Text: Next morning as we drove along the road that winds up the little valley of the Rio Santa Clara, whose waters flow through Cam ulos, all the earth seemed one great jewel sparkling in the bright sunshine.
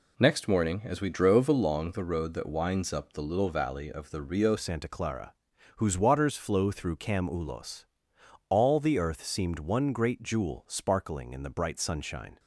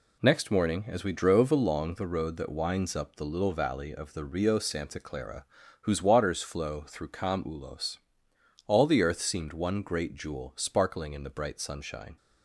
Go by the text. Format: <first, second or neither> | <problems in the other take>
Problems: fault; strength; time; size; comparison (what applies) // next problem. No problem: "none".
second | changes voice at "Santa"; from 4.5 s on; 7.8 s long